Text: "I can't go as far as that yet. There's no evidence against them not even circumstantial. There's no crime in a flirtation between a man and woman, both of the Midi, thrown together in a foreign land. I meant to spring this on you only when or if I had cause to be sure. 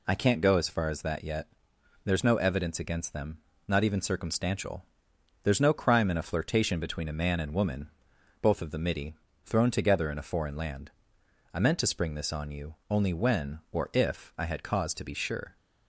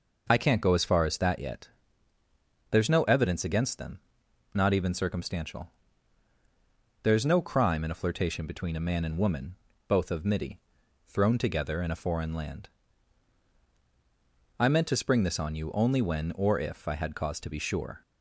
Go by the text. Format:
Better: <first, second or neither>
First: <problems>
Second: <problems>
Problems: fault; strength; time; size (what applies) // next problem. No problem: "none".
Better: first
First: pauses between "them" and "not"; slight; at 3.3 s; 0.30 s long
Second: pauses between "them" and "not"; noticeable; at 3.9 s; 0.54 s long // skips "the"; at 10.2 s